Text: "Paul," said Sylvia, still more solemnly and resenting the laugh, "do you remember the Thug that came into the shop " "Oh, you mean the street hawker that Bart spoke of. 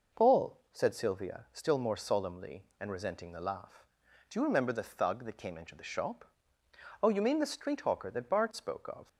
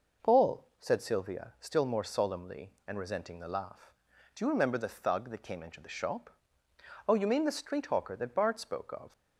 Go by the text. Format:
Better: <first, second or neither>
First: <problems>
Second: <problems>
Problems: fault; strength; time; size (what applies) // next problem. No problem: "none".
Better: neither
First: none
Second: none